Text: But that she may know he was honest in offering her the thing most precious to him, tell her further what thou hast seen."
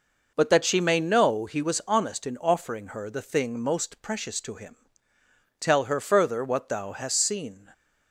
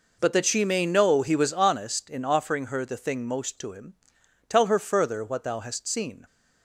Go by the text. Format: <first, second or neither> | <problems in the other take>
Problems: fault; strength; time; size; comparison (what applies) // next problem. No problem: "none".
first | skips "precious"; at 3.5 s